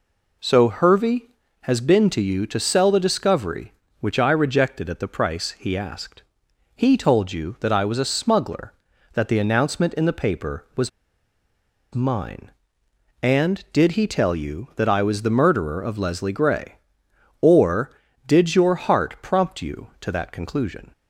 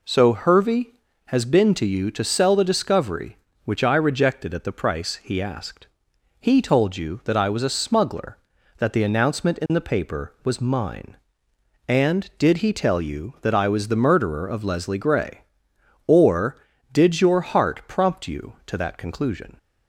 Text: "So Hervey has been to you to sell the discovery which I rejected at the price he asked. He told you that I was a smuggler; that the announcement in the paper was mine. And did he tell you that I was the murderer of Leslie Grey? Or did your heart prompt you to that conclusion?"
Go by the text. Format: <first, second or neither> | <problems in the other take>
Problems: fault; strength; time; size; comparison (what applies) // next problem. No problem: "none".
second | pauses between "was" and "mine"; at 10.8 s; 1.0 s long